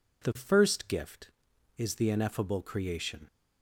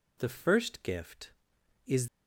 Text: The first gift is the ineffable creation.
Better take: first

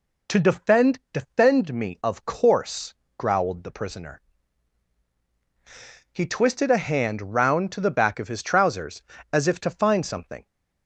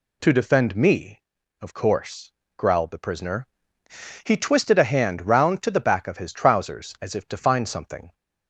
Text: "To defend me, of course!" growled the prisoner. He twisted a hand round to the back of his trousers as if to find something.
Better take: second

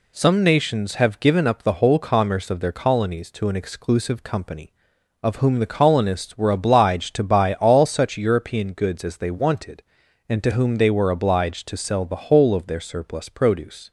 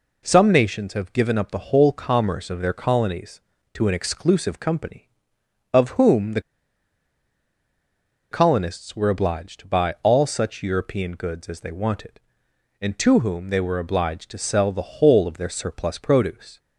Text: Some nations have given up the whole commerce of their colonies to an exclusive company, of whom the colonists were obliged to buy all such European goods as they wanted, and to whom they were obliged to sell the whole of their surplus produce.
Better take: first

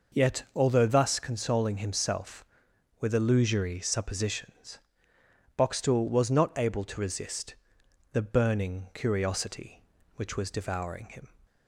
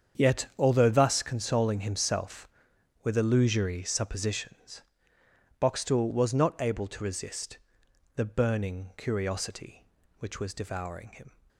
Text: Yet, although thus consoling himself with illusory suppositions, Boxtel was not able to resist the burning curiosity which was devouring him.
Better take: first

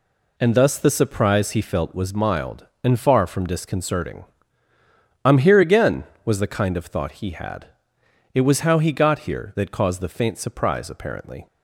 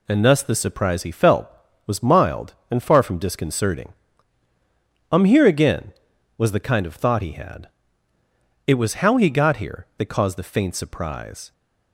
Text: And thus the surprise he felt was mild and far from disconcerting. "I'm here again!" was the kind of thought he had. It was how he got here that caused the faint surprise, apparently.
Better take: first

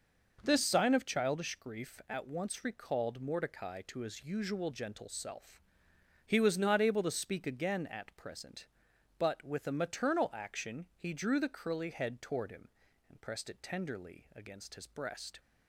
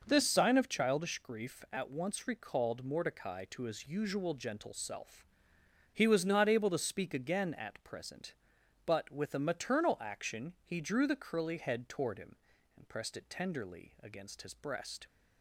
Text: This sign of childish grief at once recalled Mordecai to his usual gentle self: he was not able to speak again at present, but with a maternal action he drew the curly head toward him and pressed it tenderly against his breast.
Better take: neither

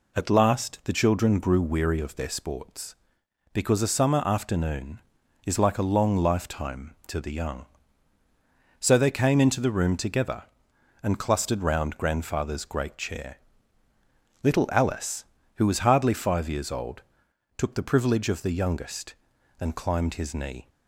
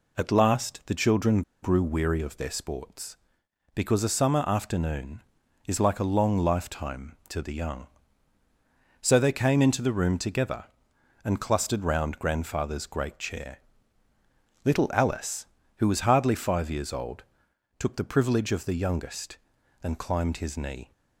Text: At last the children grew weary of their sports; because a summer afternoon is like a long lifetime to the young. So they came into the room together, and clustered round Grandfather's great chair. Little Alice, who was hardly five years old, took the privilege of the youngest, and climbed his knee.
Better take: first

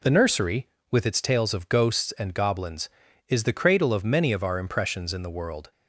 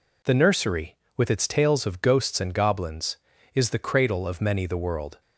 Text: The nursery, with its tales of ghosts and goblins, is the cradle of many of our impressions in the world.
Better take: first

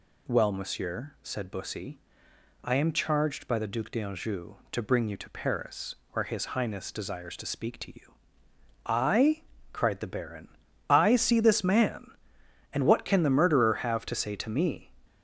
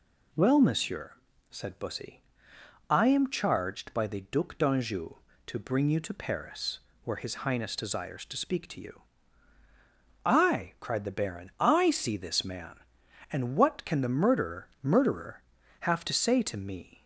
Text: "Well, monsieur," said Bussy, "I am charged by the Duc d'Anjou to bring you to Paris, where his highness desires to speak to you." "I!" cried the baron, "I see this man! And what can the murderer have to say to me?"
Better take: first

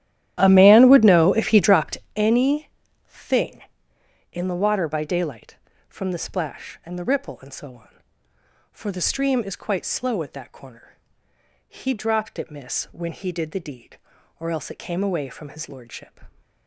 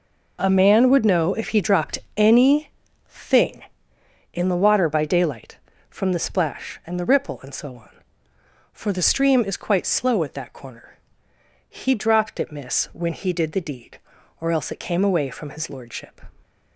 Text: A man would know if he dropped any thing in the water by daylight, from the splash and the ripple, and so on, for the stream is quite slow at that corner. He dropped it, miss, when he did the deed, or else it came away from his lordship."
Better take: second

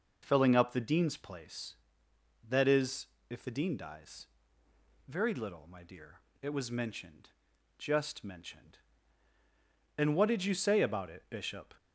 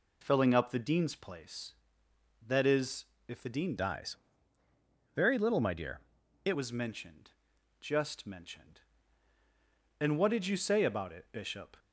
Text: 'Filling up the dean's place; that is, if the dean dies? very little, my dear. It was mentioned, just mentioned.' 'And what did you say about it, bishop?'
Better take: first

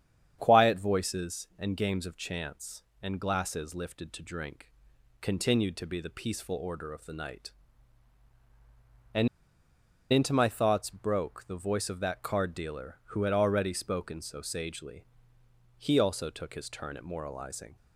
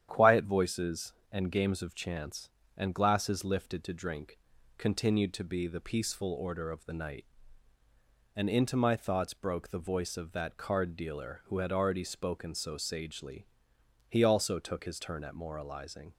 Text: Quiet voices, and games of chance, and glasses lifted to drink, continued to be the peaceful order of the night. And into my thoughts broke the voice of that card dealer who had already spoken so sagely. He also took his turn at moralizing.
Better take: second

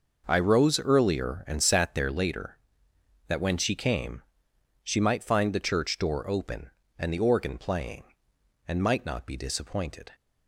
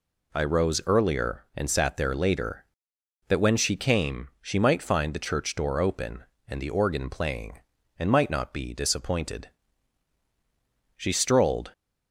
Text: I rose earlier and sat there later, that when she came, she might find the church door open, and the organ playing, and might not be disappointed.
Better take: first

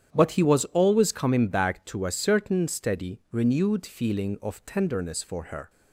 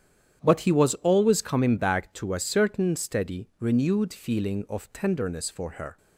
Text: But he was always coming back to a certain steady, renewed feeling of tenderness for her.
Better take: neither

